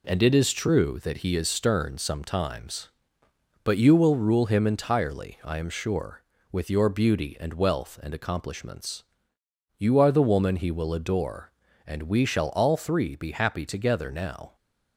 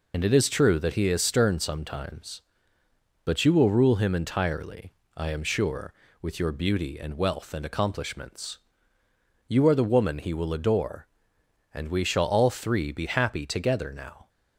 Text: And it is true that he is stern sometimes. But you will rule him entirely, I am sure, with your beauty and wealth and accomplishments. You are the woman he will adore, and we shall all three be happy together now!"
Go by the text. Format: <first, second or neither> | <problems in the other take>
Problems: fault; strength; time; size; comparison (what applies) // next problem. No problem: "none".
first | loses the start of "And"; at 0.1 s; 40 ms